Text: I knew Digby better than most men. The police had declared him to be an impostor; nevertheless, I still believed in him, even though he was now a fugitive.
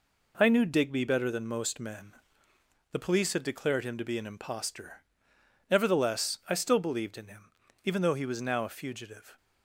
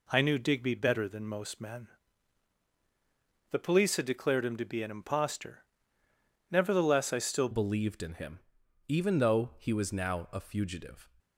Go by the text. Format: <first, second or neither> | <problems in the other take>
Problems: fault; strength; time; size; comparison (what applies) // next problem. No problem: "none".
first | changes voice at "believed"; from 7.5 s on; 3.5 s long